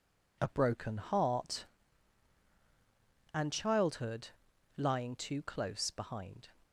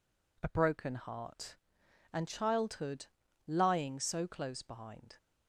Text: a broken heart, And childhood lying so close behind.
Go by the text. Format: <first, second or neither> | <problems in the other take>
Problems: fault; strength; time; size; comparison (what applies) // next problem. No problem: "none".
second | pauses between "childhood" and "lying"; noticeable; at 4.2 s; 0.48 s long; also in the second // says "too" for "so"; at 5.1 s